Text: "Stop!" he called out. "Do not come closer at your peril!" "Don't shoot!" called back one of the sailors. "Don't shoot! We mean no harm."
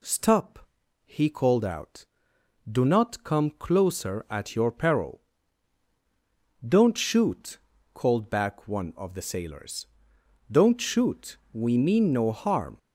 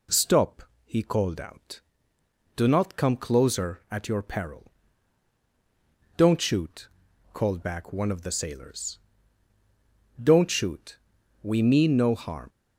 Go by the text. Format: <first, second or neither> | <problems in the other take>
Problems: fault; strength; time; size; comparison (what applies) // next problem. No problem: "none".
neither | none